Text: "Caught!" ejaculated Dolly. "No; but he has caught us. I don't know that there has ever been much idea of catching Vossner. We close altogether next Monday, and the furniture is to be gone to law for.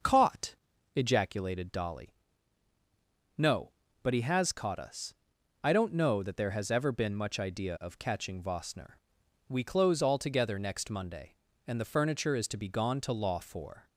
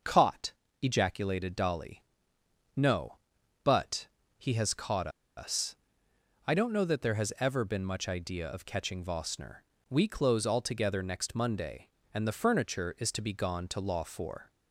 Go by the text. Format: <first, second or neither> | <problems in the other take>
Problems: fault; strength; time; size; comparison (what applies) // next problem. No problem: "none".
first | starts louder than the rest; noticeable; until 1.3 s; 6 dB; noticeable in the first // pauses between "but" and "he"; slight; at 4.0 s; 0.30 s long // pauses between "caught" and "us"; slight; at 5.0 s; 0.28 s long